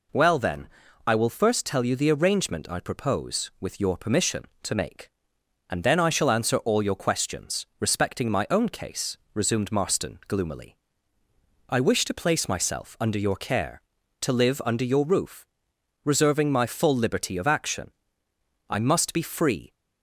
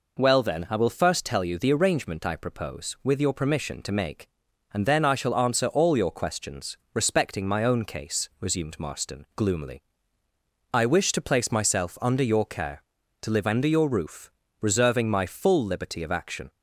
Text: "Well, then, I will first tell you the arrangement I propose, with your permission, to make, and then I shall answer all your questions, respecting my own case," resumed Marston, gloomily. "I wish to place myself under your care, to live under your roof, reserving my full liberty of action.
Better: second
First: goes on to say "I must be free"; noticeable; from 18.7 s on; 1.0 s long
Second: none

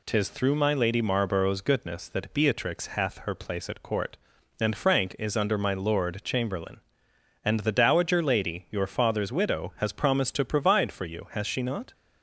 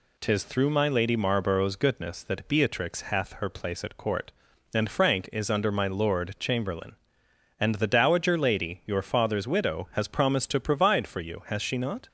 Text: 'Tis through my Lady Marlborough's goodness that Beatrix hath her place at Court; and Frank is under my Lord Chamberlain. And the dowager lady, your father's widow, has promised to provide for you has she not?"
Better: neither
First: none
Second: none

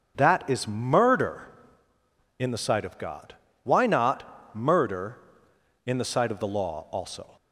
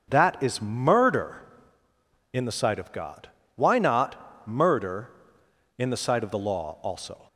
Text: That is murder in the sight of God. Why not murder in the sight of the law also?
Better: neither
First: starts louder than the rest; until 1.1 s; 7 dB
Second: starts louder than the rest; until 1.0 s; 7 dB

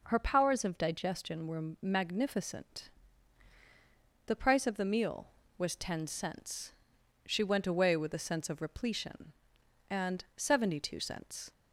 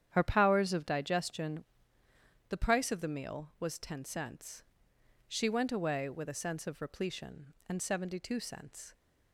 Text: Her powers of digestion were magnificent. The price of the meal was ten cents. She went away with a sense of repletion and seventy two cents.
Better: first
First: none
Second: starts louder than the rest; strong; until 1.1 s; 9.5 dB // skips "were magnificent"; at 2.0 s

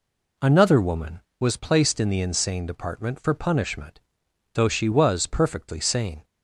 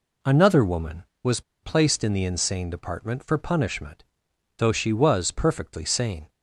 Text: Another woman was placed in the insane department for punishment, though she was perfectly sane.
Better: first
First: none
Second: pauses between "was" and "placed"; slight; at 1.4 s; 0.21 s long

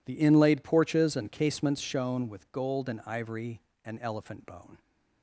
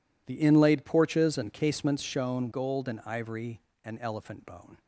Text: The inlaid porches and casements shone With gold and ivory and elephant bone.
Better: first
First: none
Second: skips "With"; at 2.5 s

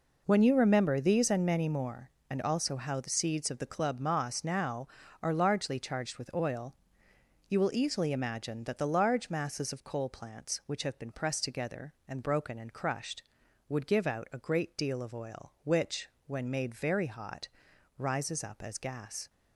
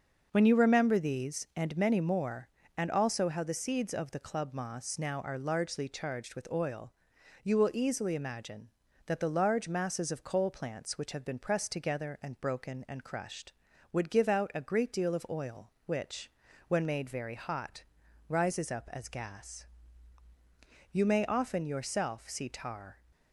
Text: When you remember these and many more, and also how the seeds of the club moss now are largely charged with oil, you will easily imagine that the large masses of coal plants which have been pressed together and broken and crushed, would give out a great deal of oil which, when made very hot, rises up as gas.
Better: first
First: none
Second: starts louder than the rest; until 1.3 s; 6 dB // goes on to say "You may often yourself see tar"; strong; from 20.9 s on; 2.0 s long

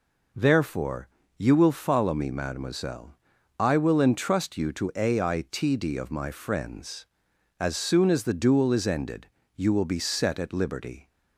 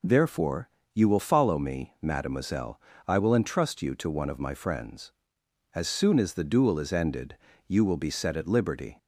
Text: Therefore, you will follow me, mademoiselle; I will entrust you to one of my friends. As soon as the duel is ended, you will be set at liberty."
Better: second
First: says "aitd" for "one"; at 4.9 s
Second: none

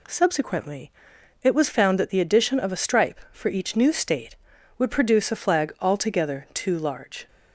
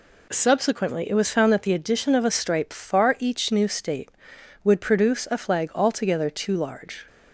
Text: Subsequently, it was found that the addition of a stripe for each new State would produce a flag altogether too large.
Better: first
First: none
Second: says "far" for "for"; at 2.7 s

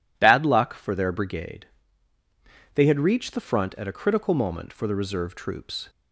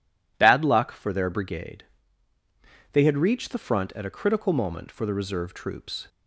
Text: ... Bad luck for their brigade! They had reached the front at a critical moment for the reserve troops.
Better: neither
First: none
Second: none

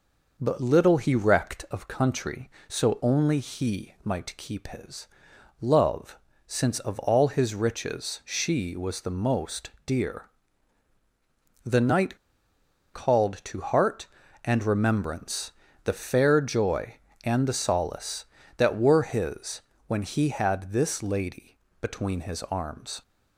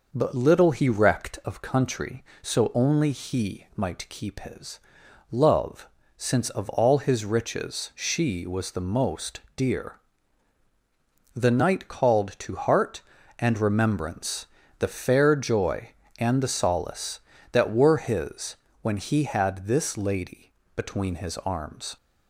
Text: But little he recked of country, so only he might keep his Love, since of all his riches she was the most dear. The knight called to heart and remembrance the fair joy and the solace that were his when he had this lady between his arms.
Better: second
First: pauses between "his" and "Love"; noticeable; at 5.0 s; 0.52 s long // pauses between "most" and "dear"; slight; at 9.7 s; 0.16 s long // pauses between "knight" and "called"; noticeable; at 12.1 s; 0.77 s long // pauses between "remembrance" and "the"; slight; at 15.5 s; 0.32 s long // pauses between "his" and "when"; slight; at 19.6 s; 0.24 s long // pauses between "lady" and "between"; slight; at 21.5 s; 0.22 s long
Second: pauses between "his" and "Love"; noticeable; at 4.8 s; 0.50 s long // pauses between "most" and "dear"; slight; at 9.4 s; 0.16 s long // pauses between "remembrance" and "the"; slight; at 14.4 s; 0.32 s long // pauses between "his" and "when"; slight; at 18.5 s; 0.24 s long // pauses between "lady" and "between"; slight; at 20.5 s; 0.22 s long

